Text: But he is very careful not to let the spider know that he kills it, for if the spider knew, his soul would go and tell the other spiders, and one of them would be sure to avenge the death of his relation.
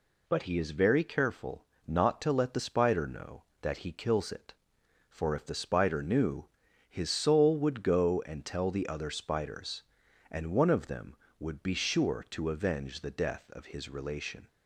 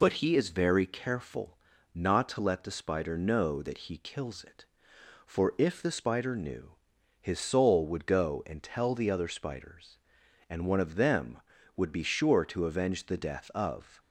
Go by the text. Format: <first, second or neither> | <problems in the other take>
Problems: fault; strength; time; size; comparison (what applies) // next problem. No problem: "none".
first | pauses between "careful" and "not"; slight; at 1.5 s; 0.34 s long; slight in the first // stops before "his relation"; at 13.9 s